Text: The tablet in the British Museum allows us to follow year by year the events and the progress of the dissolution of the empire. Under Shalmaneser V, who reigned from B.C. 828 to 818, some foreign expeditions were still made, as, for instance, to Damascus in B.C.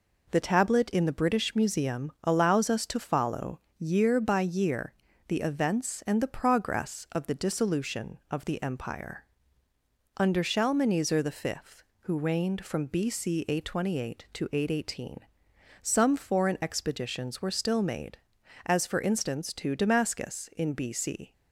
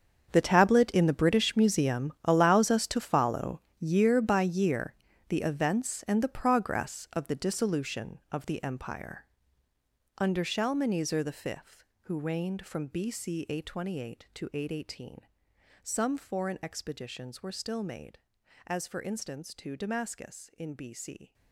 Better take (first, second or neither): first